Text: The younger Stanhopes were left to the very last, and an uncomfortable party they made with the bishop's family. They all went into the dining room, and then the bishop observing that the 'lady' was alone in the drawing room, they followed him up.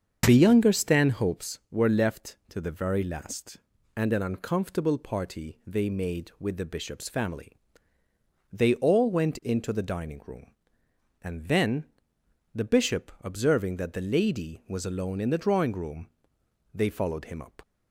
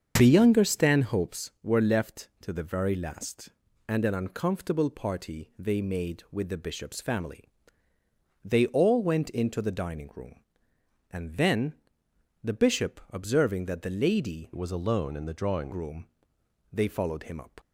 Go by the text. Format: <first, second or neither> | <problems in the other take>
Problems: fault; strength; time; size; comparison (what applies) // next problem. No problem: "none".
first | starts louder than the rest; until 1.1 s; 7 dB; also in the first // pauses between "then" and "the"; noticeable; at 11.7 s; 0.68 s long; noticeable in the first // changes voice from "was" to "drawing"; from 14.5 to 15.7 s; 1.2 s long